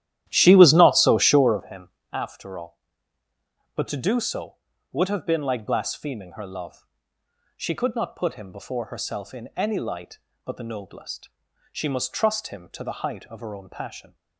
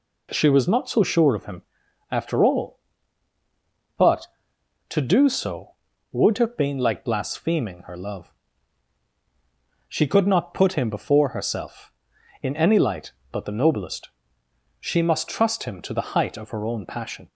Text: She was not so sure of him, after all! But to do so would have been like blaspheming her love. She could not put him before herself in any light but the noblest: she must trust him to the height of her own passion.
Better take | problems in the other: second | starts louder than the rest; strong; until 1.7 s; 12.5 dB

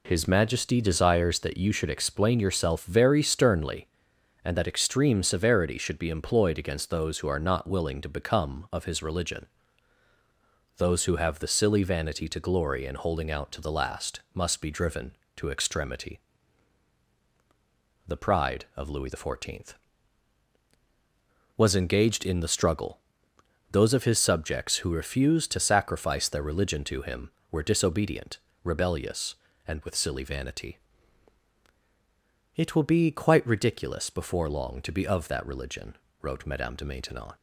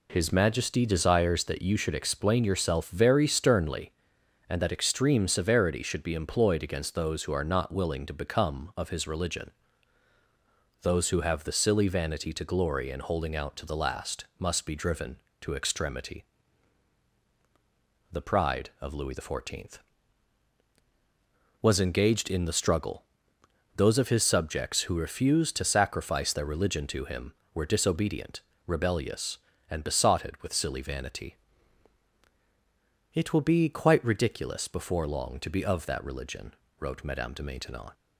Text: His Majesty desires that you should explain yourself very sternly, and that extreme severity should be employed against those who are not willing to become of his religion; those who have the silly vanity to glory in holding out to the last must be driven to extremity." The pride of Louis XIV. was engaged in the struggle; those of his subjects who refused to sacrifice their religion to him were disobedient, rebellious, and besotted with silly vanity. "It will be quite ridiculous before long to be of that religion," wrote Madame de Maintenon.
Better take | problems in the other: second | skips "besotted"; at 29.8 s

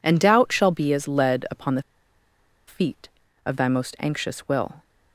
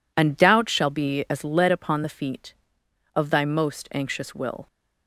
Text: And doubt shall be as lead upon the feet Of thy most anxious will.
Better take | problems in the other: second | pauses between "the" and "feet"; noticeable; at 1.8 s; 0.84 s long

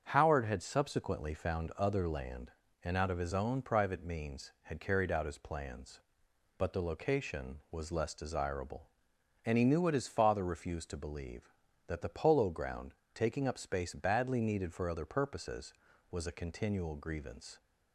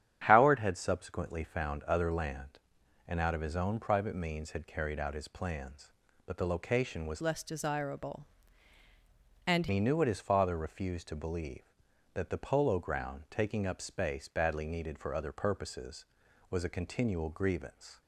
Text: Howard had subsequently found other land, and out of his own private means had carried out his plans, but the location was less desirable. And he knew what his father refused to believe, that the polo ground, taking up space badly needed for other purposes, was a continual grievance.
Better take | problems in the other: first | starts louder than the rest; strong; until 1.2 s; 9.5 dB; strong in the first // changes voice from "less" to "And"; from 7.2 to 9.6 s; 2.4 s long

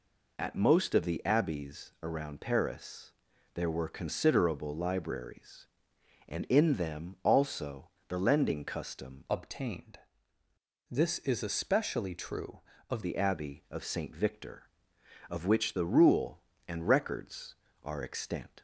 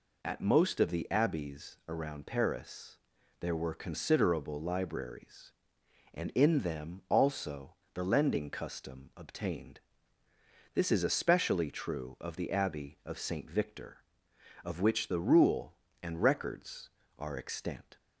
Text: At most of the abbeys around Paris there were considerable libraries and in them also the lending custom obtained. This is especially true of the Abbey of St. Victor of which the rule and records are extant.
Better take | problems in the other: second | pauses between "Paris" and "there"; at 3.1 s; 0.40 s long; also in the second // pauses between "also" and "the"; slight; at 7.9 s; 0.18 s long; slight in the second // changes voice from "obtained" to "of"; from 9.2 to 13.0 s; 3.8 s long

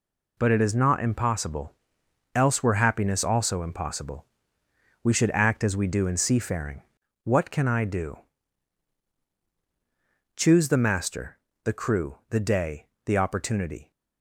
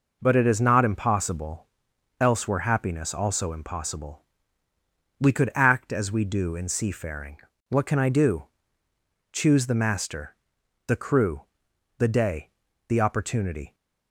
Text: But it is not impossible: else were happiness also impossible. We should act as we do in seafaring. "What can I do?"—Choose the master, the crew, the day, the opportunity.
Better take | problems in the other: first | says "could" for "should"; at 5.3 s

